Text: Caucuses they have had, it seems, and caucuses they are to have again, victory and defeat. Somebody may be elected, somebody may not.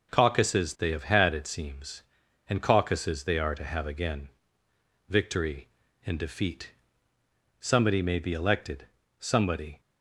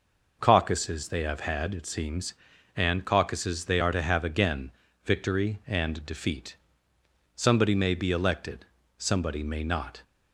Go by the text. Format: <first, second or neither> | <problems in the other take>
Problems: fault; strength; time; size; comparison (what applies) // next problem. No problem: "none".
second | stops before "may not"; at 9.7 s